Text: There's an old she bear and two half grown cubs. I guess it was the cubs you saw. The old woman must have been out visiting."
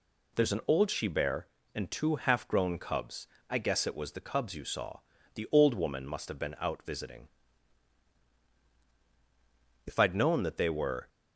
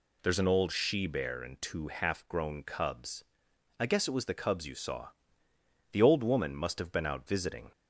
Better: second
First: goes on to say "If I'd known that they were"; noticeable; from 9.8 s on; 1.2 s long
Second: none

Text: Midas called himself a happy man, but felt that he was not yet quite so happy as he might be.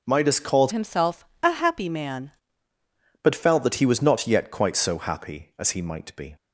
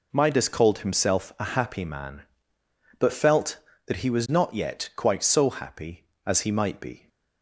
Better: second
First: changes voice from "himself" to "man"; from 0.7 to 2.3 s; 1.6 s long // pauses between "himself" and "a"; slight; at 1.2 s; 0.16 s long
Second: none

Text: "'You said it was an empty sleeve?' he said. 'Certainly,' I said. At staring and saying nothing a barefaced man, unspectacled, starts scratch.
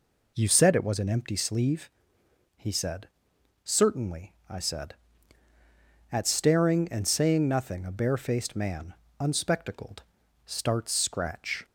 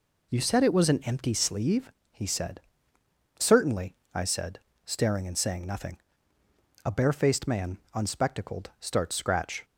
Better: first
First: none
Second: skips "At"; at 4.7 s // pauses between "nothing" and "a"; noticeable; at 5.9 s; 0.88 s long

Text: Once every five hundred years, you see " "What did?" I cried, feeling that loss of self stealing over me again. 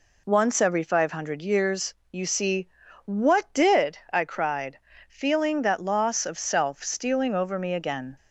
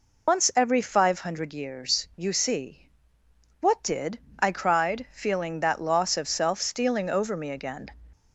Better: first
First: none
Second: loses the start of "Once"; at 0.2 s; 115 ms

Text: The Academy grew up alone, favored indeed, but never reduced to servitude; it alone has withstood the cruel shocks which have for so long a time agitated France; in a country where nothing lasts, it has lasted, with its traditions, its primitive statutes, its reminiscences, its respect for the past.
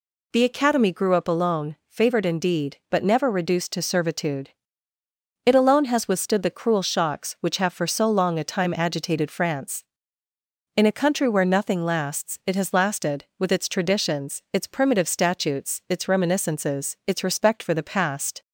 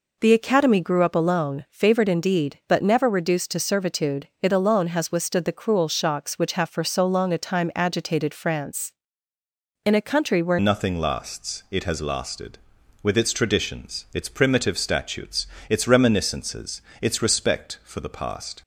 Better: first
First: none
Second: changes voice at "nothing"; from 10.5 s on; 8.1 s long

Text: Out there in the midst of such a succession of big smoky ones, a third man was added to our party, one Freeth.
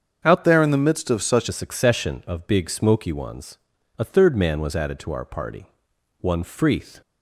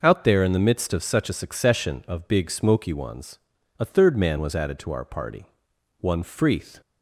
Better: second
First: starts louder than the rest; until 1.2 s; 7 dB // changes voice from "there" to "such"; from 0.4 to 1.4 s; 1.0 s long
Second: none

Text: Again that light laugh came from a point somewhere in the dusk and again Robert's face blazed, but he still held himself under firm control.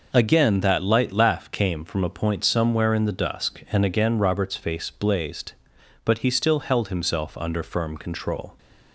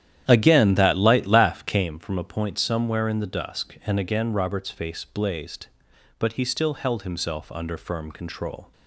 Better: first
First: none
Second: starts louder than the rest; strong; until 1.9 s; 10.5 dB

